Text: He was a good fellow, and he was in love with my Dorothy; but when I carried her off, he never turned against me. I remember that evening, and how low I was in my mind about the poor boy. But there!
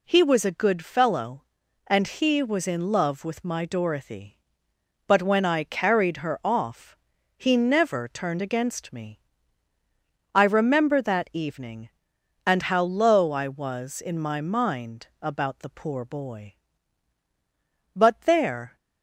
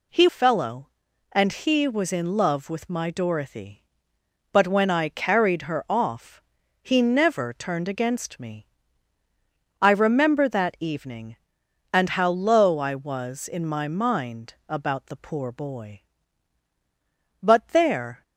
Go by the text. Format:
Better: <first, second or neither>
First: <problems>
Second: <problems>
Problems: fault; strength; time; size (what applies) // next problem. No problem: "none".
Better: first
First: none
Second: skips "was a good"; at 0.2 s